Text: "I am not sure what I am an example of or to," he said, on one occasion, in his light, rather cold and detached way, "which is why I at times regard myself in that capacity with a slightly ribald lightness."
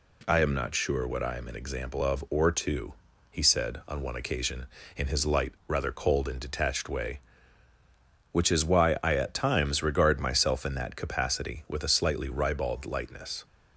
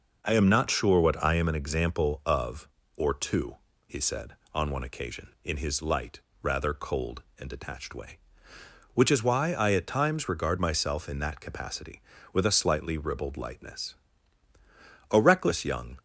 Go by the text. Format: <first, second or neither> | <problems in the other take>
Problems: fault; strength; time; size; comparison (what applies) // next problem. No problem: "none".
first | goes on to say "A reckless young"; noticeable; from 15.1 s on; 0.86 s long